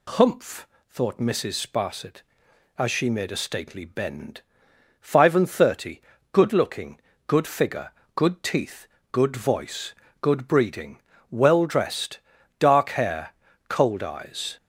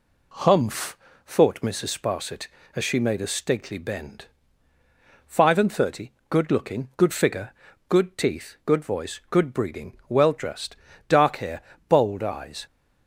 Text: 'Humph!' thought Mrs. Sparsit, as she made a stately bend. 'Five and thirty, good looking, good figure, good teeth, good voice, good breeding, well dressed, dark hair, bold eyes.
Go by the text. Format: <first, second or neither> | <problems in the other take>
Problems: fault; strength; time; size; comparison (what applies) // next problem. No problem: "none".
second | says "cold" for "bold"; at 13.6 s